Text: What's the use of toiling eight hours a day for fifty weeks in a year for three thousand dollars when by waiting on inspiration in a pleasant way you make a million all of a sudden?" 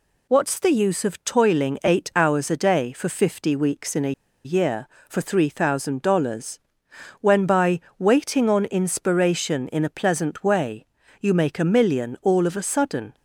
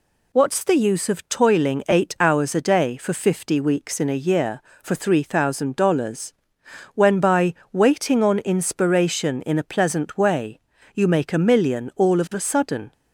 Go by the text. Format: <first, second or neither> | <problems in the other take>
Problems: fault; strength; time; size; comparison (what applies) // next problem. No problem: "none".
second | pauses between "a" and "year"; slight; at 4.1 s; 0.33 s long // pauses between "dollars" and "when"; noticeable; at 6.5 s; 0.62 s long; noticeable in the second // pauses between "by" and "waiting"; slight; at 7.7 s; 0.22 s long; slight in the second // pauses between "way" and "you"; slight; at 10.8 s; 0.36 s long; slight in the second